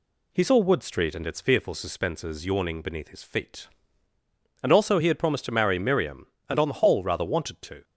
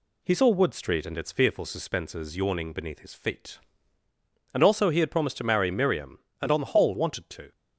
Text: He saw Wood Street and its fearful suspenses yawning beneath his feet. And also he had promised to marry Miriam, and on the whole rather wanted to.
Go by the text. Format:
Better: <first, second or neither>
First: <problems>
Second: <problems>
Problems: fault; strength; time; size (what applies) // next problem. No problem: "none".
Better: first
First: none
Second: skips "rather"; at 6.9 s